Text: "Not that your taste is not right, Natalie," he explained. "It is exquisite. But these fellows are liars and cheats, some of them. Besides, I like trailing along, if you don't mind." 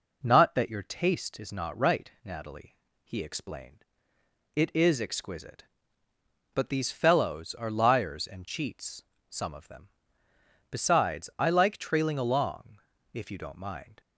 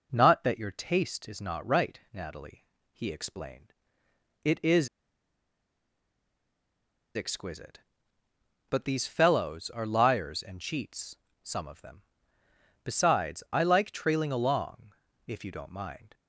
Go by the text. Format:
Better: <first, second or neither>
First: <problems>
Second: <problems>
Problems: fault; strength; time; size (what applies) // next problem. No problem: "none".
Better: first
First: none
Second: pauses between "is" and "exquisite"; strong; at 4.8 s; 2.2 s long